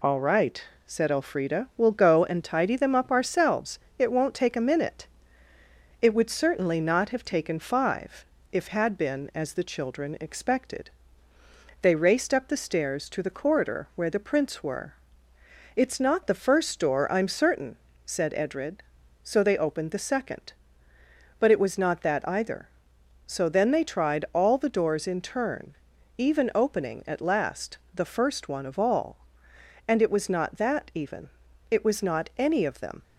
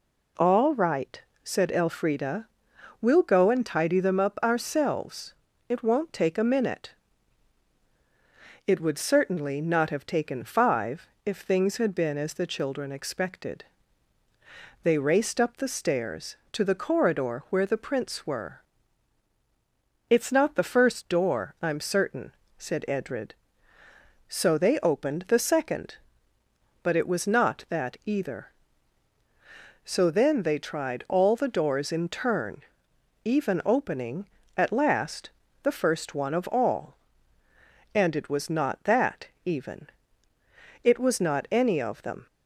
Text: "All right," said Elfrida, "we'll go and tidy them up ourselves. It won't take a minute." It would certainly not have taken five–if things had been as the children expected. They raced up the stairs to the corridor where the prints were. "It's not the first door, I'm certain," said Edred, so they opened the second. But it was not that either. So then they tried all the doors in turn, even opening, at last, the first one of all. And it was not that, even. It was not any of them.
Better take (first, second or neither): second